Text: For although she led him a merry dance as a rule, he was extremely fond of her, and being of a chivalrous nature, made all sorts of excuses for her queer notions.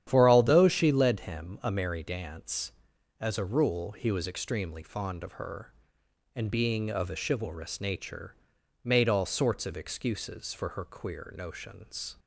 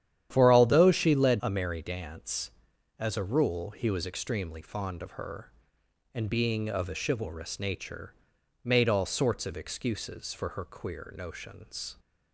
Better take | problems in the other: first | starts louder than the rest; strong; until 1.3 s; 10.5 dB; strong in the first // skips "him"; at 1.4 s

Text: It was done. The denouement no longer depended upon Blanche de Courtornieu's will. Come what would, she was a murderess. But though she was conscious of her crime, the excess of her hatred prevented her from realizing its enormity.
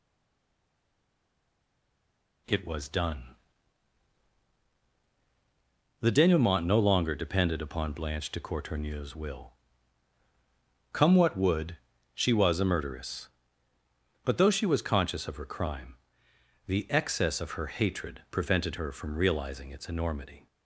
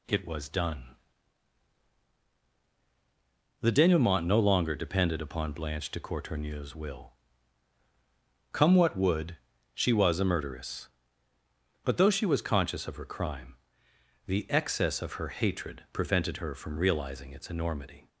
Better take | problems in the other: second | stays silent before the first word; until 2.4 s; 2.4 s long

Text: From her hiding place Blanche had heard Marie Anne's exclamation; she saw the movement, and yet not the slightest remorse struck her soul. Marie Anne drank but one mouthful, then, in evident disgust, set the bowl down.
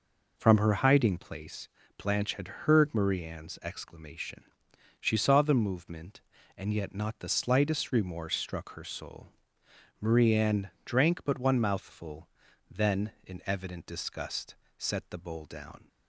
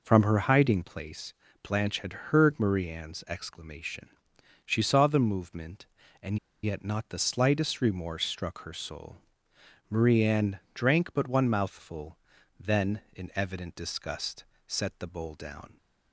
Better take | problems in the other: first | pauses between "place" and "Blanche"; slight; at 1.3 s; 0.34 s long; slight in the first // pauses between "and" and "yet"; slight; at 6.3 s; 0.26 s long

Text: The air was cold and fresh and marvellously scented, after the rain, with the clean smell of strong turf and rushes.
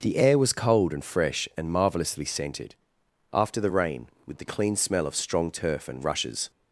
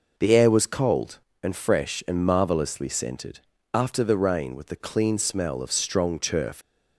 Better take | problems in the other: first | stops before "and rushes"; at 6.6 s

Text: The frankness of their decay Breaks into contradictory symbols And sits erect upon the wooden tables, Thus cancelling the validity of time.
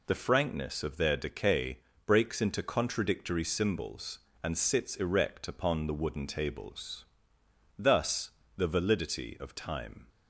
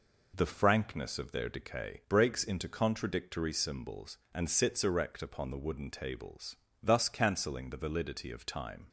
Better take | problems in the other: second | pauses between "decay" and "Breaks"; slight; at 1.7 s; 0.30 s long // skips "cancelling"; at 8.4 s

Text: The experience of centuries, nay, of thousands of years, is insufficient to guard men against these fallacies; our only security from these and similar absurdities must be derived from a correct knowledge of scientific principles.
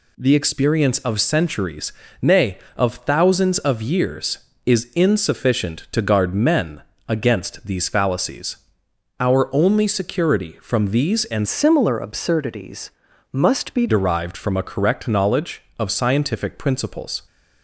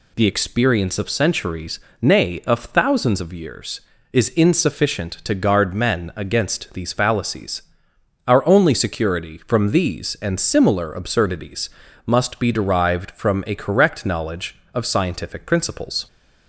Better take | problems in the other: second | pauses between "men" and "against"; slight; at 6.8 s; 0.26 s long // changes voice from "similar" to "be"; from 11.4 to 13.8 s; 2.4 s long // pauses between "absurdities" and "must"; at 12.9 s; 0.40 s long; slight in the second

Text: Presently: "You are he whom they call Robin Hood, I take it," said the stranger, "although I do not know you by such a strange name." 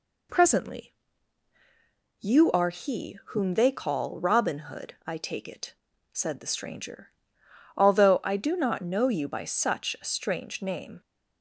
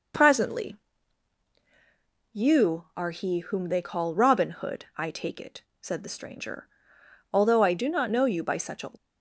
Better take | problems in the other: first | stops before "strange name"; at 8.9 s

